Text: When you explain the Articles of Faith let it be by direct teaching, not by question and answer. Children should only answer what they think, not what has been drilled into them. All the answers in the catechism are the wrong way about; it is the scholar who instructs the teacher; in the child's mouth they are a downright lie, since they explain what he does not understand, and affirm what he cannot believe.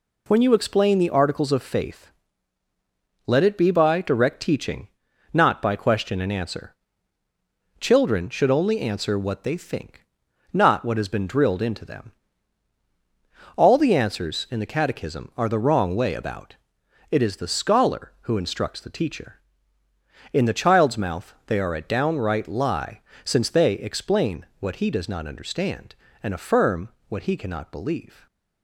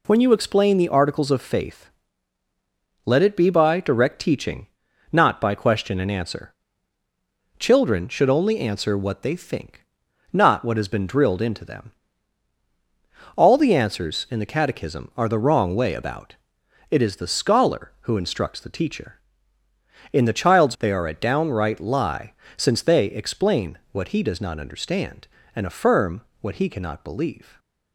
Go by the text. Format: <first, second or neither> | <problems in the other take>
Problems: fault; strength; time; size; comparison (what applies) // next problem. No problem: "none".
first | pauses between "Faith" and "let"; at 1.8 s; 1.1 s long; also in the first // skips "mouth"; at 20.7 s // pauses between "affirm" and "what"; slight; at 26.2 s; 0.22 s long; slight in the first